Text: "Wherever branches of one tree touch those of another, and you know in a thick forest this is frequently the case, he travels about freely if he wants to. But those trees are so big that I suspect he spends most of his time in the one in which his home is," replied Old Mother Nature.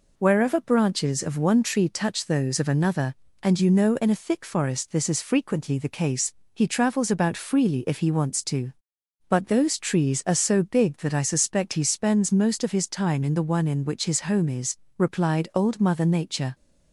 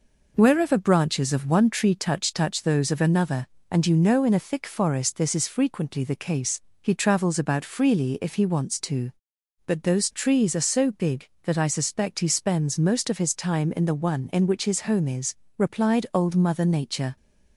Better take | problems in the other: first | says "touch" twice; at 2.3 s

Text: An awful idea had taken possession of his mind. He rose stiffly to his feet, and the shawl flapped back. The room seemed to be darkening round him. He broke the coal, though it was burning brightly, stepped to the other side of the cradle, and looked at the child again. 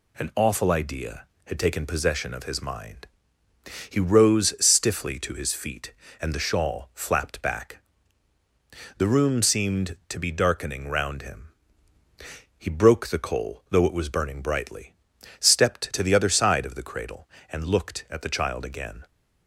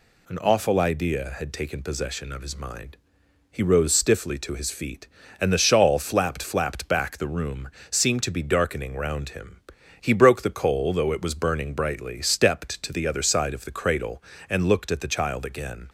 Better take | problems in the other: first | says "flapped" twice; at 6.4 s // pauses between "room" and "seemed"; slight; at 7.6 s; 0.20 s long

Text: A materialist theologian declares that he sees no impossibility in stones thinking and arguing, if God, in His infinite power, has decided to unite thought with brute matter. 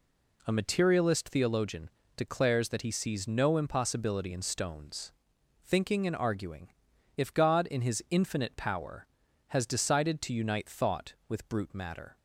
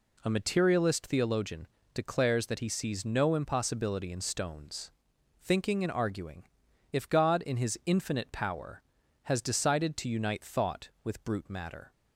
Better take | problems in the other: neither | pauses between "theologian" and "declares"; slight; the same in both // pauses between "stones" and "thinking"; noticeable; the same in both

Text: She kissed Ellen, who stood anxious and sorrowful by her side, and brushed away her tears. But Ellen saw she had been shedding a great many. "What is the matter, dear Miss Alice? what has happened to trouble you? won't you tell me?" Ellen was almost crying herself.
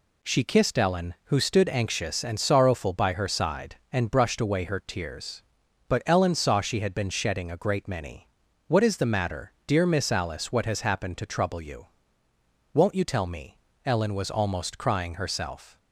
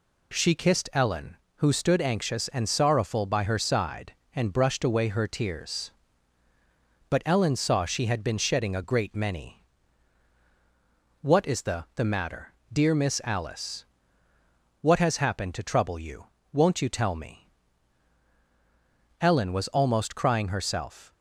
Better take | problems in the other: first | says "the" twice; at 11.9 s

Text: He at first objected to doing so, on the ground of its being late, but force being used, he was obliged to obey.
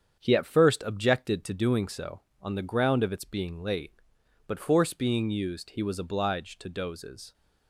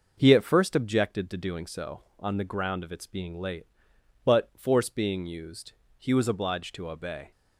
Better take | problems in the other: second | starts louder than the rest; strong; until 1.2 s; 7.5 dB // says "dozes" for "obey"; at 6.6 s

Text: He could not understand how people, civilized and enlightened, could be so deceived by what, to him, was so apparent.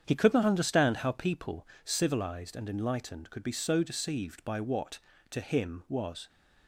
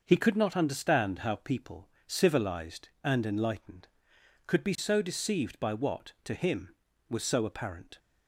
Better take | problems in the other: second | starts louder than the rest; strong; until 1.0 s; 8 dB // stops before "so apparent"; at 6.2 s

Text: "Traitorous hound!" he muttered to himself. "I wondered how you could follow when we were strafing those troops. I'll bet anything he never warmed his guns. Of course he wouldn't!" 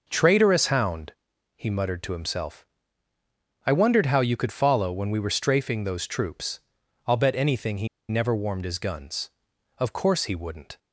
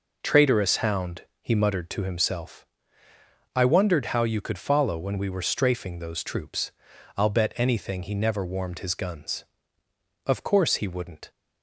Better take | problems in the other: second | pauses between "he" and "never"; slight; at 7.8 s; 0.22 s long

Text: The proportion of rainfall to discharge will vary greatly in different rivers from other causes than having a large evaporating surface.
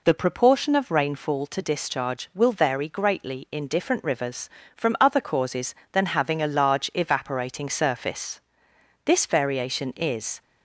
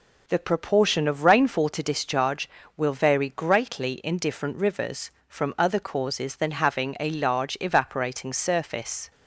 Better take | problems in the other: second | goes on to say "This variation is"; from 9.0 s on; 1.3 s long

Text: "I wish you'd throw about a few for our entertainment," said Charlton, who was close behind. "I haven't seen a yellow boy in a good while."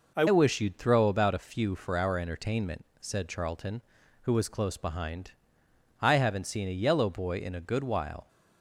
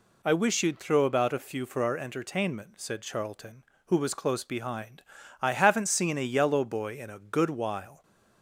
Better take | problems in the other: second | changes voice at "wish"; from 0.2 s on; 8.0 s long

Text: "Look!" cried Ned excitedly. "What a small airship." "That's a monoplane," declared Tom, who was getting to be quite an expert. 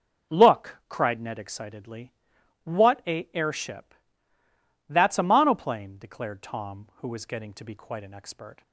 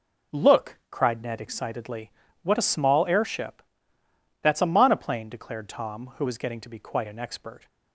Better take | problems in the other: second | skips "small"; at 3.3 s

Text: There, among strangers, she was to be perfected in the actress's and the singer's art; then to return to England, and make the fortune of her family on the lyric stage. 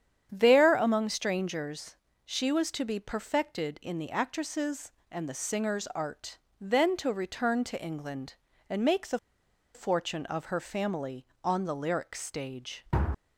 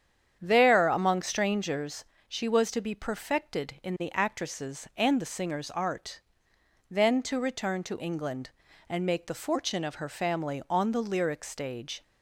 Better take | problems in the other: second | starts louder than the rest; strong; until 1.3 s; 9 dB; strong in the second // pauses between "the" and "fortune"; noticeable; at 9.1 s; 0.56 s long

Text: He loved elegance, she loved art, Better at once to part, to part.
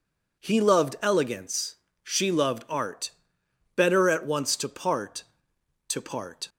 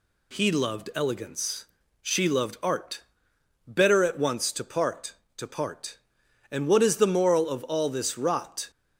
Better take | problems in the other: first | goes on to say "And what is the moral of all this rot"; strong; from 6.5 s on; 2.1 s long

